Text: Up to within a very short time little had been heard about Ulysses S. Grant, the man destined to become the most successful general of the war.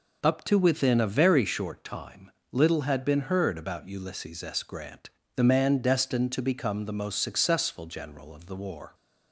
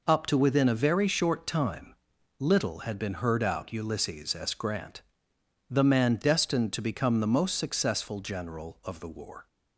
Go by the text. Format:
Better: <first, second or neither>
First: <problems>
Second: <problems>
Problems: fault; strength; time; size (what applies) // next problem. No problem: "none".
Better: first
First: pauses between "time" and "little"; slight; at 2.3 s; 0.18 s long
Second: pauses between "time" and "little"; noticeable; at 1.9 s; 0.46 s long // says "out" for "about"; at 3.4 s